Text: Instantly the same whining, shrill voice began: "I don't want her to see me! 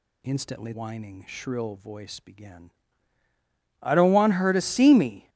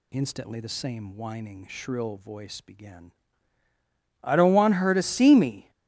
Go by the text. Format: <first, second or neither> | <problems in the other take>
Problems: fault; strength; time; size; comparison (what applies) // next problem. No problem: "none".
second | skips "the same"; at 0.7 s